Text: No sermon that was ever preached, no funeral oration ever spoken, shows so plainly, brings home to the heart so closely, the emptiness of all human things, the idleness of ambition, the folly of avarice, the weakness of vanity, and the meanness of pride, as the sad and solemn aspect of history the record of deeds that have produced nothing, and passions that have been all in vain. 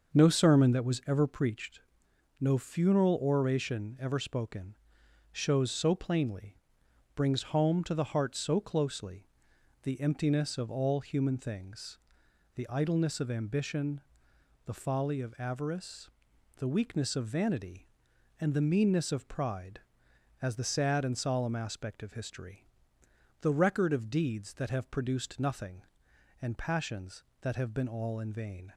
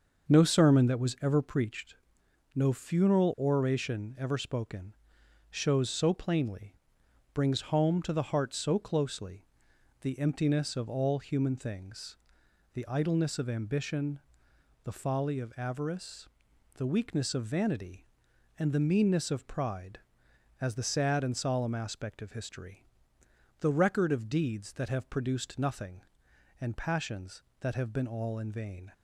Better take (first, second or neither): neither